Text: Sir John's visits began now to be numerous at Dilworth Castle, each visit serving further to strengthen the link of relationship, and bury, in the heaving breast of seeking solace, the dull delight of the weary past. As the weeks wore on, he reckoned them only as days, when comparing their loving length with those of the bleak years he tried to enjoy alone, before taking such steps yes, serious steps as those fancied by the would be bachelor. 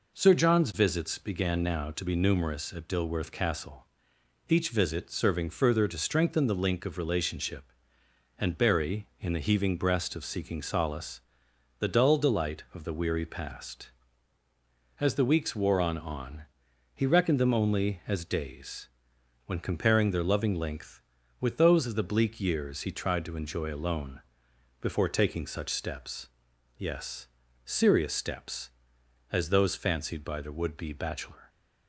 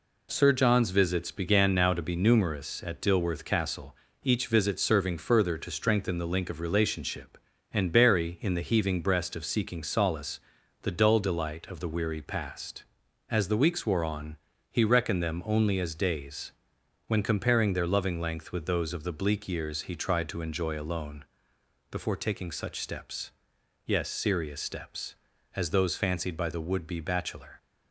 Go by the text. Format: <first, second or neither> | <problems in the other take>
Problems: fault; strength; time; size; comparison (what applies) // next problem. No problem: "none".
second | says "on" twice; at 15.9 s // pauses between "steps" and "yes"; noticeable; at 26.2 s; 0.48 s long; noticeable in the second